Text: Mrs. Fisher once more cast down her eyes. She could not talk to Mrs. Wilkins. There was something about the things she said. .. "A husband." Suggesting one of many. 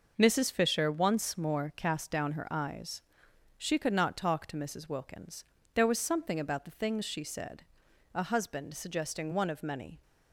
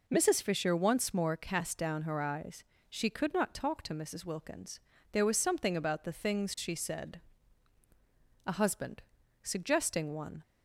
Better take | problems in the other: first | stops before "of many"; at 10.4 s

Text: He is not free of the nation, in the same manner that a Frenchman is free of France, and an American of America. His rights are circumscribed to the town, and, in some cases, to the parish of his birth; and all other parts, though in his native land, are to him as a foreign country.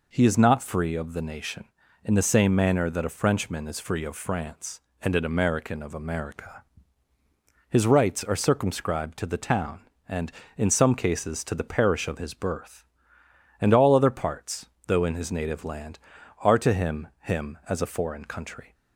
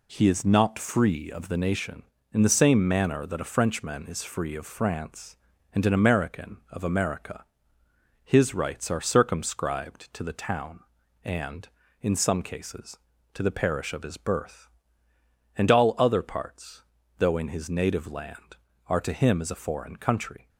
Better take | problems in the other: second | says "him" twice; at 17.2 s

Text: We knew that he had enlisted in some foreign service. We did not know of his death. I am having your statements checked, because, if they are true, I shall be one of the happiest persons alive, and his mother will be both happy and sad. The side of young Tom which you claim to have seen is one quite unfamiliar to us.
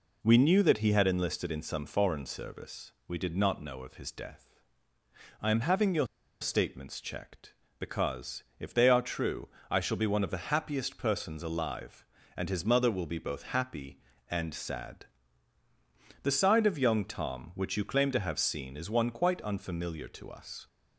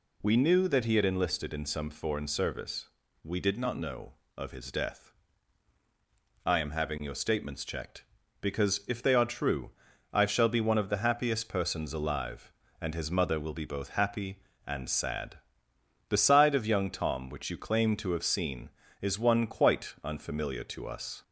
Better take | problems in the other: second | pauses between "your" and "statements"; slight; at 6.0 s; 0.34 s long

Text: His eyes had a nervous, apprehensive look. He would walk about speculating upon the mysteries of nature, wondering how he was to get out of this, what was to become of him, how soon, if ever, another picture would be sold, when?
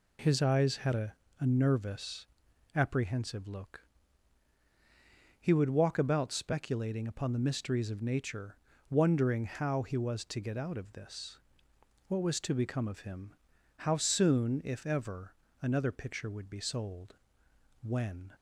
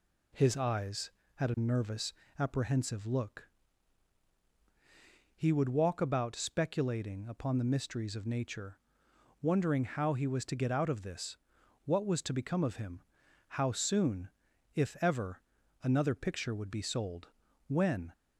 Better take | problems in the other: second | says "a" twice; at 1.3 s

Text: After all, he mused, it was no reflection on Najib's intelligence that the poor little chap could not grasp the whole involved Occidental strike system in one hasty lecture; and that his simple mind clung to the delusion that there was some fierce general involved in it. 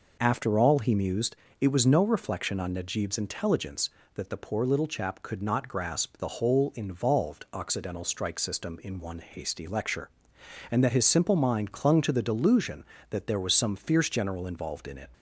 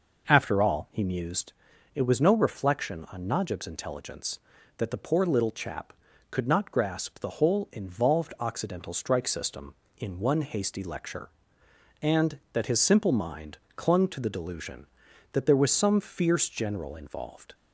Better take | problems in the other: first | pauses between "mind" and "clung"; slight; at 13.5 s; 0.18 s long // stops before "in it"; at 17.5 s

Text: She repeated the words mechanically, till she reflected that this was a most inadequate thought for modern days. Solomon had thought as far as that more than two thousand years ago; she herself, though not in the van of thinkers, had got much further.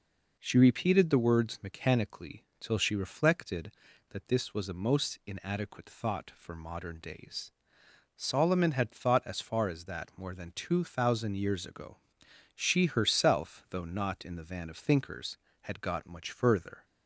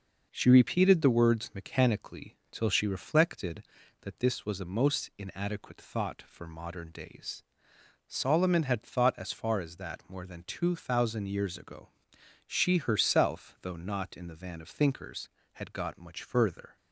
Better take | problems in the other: first | gets quieter; noticeable; throughout; 4 dB

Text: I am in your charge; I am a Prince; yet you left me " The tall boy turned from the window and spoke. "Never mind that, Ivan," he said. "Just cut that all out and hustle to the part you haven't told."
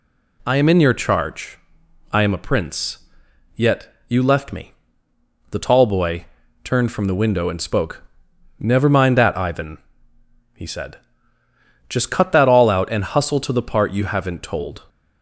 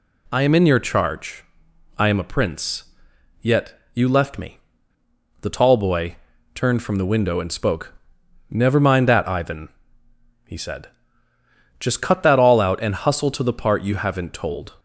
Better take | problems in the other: neither | pauses between "yet" and "you"; slight; the same in both // pauses between "boy" and "turned"; slight; the same in both

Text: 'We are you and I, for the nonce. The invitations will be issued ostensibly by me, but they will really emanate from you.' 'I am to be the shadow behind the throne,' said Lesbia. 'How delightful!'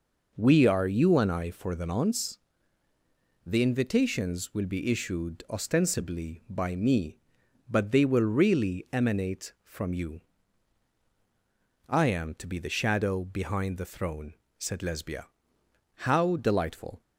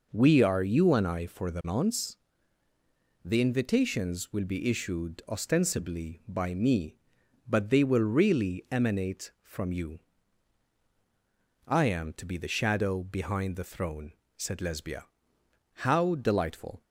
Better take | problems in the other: neither | none

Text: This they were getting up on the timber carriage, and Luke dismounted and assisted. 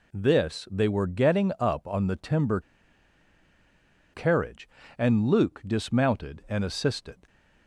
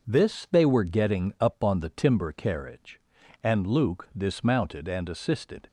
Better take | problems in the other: second | pauses between "timber" and "carriage"; strong; at 2.6 s; 1.5 s long

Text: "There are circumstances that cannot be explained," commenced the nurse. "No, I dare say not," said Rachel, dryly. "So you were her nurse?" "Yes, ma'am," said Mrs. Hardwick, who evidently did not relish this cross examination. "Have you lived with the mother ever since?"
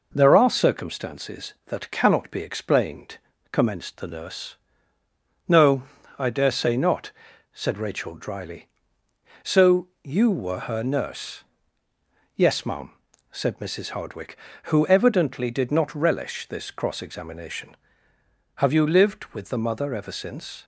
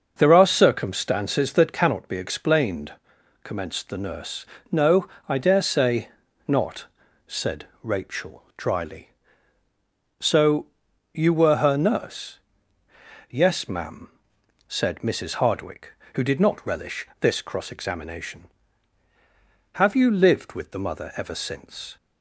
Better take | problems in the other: first | pauses between "say" and "not"; at 6.0 s; 0.40 s long // pauses between "said" and "Rachel"; slight; at 7.6 s; 0.16 s long // pauses between "So" and "you"; noticeable; at 10.6 s; 0.46 s long; slight in the first // skips "evidently"; at 16.2 s

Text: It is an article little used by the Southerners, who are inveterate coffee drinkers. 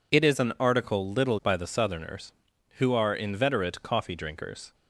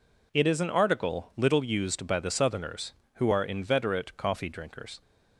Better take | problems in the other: second | skips "used"; at 1.4 s

